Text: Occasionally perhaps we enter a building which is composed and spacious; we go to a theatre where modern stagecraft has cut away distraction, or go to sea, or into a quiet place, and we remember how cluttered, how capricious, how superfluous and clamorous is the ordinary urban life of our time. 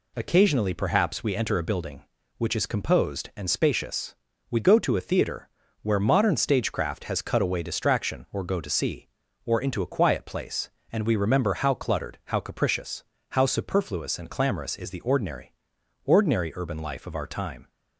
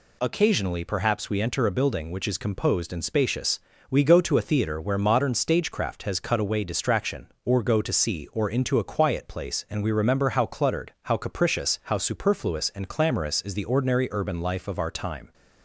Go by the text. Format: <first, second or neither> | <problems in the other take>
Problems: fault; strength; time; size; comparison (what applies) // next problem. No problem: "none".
second | pauses between "theatre" and "where"; slight; at 5.4 s; 0.34 s long // says "ordinary" twice; at 16.0 s